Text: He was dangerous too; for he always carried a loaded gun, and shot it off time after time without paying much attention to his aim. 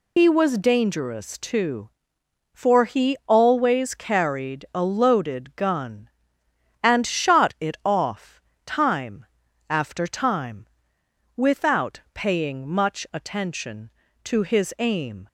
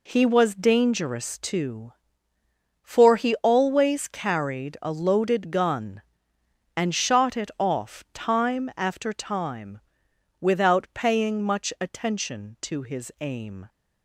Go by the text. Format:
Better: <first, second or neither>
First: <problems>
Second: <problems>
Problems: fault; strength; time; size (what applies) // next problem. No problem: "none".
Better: second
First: loses the start of "He"; at 0.1 s; 110 ms // pauses between "off" and "time"; slight; at 8.3 s; 0.26 s long // pauses between "time" and "after"; at 9.2 s; 0.42 s long // pauses between "time" and "without"; noticeable; at 10.6 s; 0.68 s long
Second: pauses between "time" and "without"; noticeable; at 9.8 s; 0.58 s long